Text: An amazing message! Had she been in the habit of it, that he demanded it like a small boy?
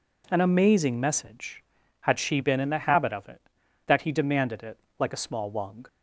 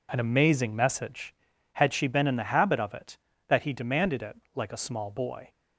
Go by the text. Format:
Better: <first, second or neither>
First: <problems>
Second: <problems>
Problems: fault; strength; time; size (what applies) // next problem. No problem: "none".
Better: second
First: pauses between "it" and "like"; slight; at 4.7 s; 0.20 s long // says "wung" for "boy"; at 5.5 s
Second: pauses between "it" and "like"; slight; at 4.3 s; 0.18 s long